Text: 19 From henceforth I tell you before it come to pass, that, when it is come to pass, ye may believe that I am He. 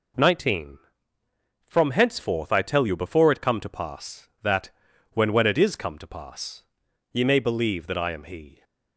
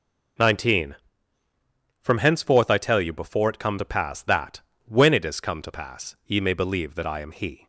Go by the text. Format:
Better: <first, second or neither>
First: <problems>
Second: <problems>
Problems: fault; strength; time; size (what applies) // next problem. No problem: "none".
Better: second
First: says "when" twice; at 5.3 s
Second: none